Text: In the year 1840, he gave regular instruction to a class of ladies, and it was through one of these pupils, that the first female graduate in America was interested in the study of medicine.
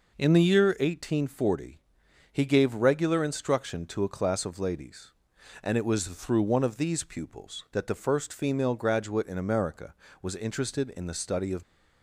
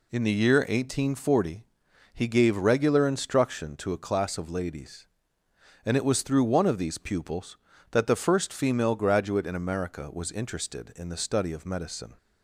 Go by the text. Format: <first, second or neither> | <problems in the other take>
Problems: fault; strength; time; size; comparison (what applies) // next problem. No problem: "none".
second | stops before "medicine"; at 11.6 s